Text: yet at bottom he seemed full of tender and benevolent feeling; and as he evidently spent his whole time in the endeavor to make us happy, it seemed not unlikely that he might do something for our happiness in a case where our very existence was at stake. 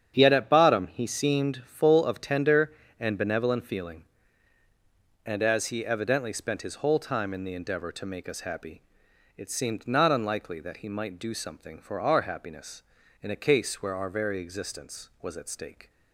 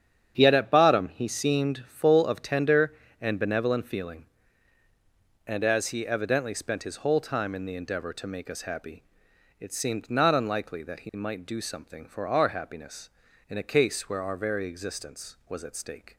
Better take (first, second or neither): neither